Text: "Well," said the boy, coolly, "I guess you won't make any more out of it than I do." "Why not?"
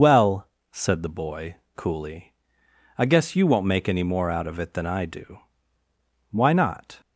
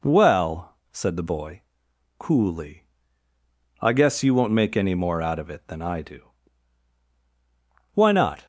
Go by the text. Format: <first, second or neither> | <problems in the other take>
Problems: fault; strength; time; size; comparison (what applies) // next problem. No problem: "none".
second | loses the start of "Well"; at 0.0 s; 60 ms